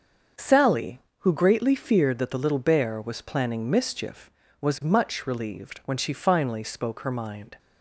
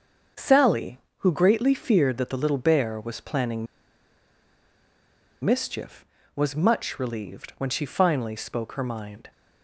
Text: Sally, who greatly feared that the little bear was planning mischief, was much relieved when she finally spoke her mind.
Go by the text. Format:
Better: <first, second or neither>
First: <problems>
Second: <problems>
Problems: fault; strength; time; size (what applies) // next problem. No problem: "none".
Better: first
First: starts louder than the rest; until 1.5 s; 6.5 dB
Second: starts louder than the rest; until 1.5 s; 6.5 dB // pauses between "planning" and "mischief"; strong; at 3.6 s; 1.7 s long